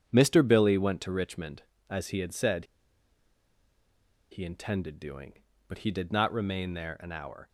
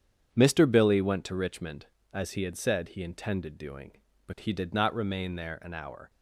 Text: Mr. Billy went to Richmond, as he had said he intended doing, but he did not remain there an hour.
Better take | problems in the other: second | starts louder than the rest; strong; until 1.0 s; 8 dB; strong in the second // pauses between "said" and "he"; strong; at 2.6 s; 1.6 s long

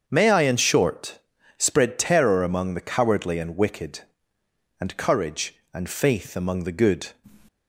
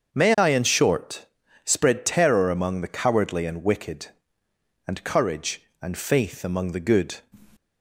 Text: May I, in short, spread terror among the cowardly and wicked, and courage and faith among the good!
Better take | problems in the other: neither | starts louder than the rest; the same in both

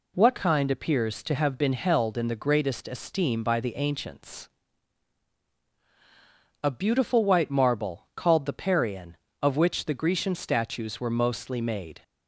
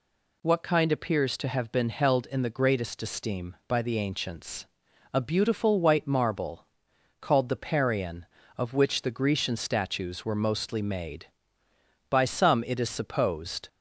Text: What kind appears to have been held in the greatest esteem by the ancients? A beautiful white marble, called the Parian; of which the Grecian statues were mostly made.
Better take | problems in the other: first | goes on to say "By some it is supposed"; from 12.0 s on; 1.5 s long

